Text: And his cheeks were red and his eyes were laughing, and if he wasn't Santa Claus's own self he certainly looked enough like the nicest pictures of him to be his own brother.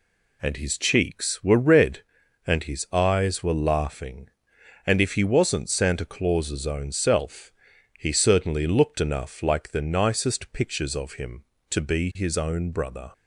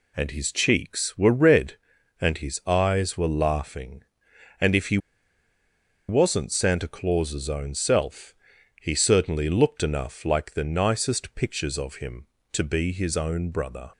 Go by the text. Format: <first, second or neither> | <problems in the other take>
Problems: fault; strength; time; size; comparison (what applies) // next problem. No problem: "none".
first | pauses between "he" and "wasn't"; at 4.9 s; 1.1 s long // pauses between "self" and "he"; noticeable; at 8.3 s; 0.46 s long; noticeable in the first